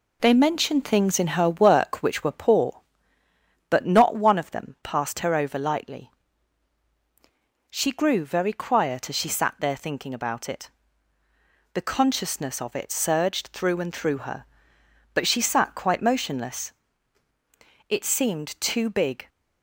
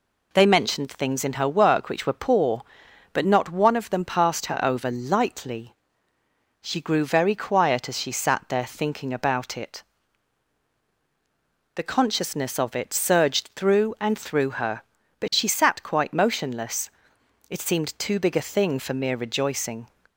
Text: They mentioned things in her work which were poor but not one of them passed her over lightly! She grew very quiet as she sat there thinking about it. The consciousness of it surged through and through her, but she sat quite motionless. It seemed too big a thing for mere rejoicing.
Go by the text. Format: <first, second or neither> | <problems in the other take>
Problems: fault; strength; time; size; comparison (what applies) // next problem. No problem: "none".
second | stops before "a thing for mere rejoicing"; at 19.2 s